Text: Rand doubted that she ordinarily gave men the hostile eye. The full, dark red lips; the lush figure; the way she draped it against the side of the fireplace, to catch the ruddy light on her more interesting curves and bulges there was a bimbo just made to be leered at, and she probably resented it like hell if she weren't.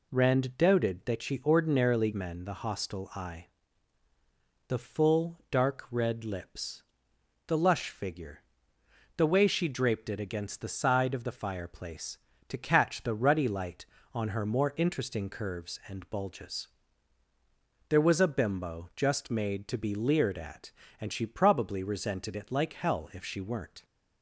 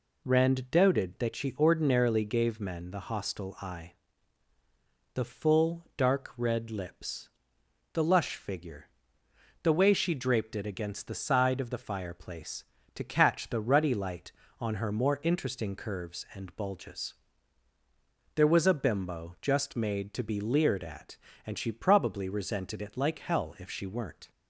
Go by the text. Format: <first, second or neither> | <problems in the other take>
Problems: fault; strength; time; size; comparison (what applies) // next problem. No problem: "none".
second | skips "gave"; at 2.1 s // pauses between "bulges" and "there"; at 16.6 s; 1.2 s long; also in the second